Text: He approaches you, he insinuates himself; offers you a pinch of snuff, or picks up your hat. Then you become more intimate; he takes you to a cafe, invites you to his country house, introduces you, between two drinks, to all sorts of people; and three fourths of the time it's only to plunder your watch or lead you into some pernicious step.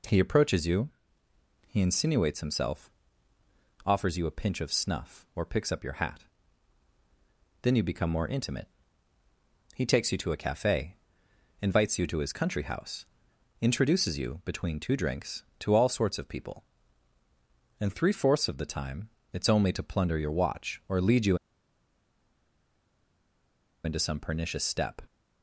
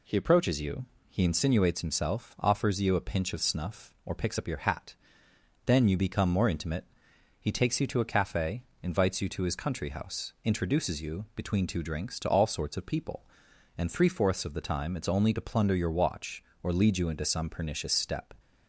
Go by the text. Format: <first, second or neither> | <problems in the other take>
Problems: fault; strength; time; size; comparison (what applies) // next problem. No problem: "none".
second | pauses between "time" and "it's"; slight; at 19.0 s; 0.24 s long // pauses between "you" and "into"; strong; at 21.3 s; 2.4 s long